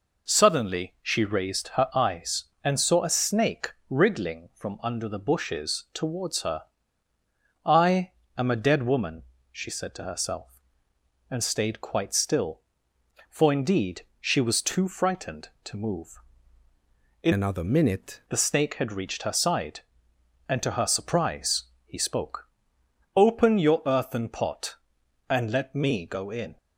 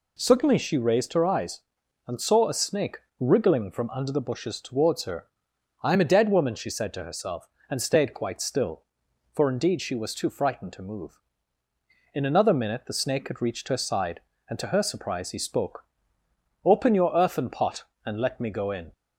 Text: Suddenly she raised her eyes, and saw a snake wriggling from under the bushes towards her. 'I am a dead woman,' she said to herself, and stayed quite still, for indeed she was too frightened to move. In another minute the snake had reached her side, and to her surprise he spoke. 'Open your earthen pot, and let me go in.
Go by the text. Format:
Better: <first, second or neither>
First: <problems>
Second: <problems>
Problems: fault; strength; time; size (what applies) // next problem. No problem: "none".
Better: second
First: pauses between "snake" and "wriggling"; slight; at 3.6 s; 0.18 s long // pauses between "I" and "am"; slight; at 8.0 s; 0.26 s long // pauses between "indeed" and "she"; slight; at 14.0 s; 0.16 s long // changes voice from "another" to "minute"; from 17.3 to 18.1 s; 0.8 s long // pauses between "surprise" and "he"; slight; at 21.6 s; 0.20 s long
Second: pauses between "snake" and "wriggling"; slight; at 2.9 s; 0.22 s long